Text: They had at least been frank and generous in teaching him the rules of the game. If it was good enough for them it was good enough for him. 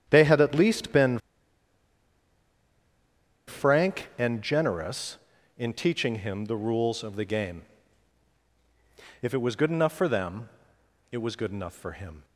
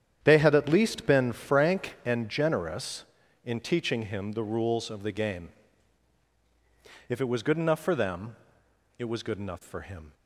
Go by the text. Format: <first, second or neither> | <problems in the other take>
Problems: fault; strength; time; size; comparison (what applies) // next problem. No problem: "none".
second | starts louder than the rest; strong; until 1.0 s; 9 dB; strong in the second // pauses between "been" and "frank"; strong; at 1.1 s; 2.2 s long // pauses between "them" and "it"; noticeable; at 10.4 s; 0.64 s long; noticeable in the second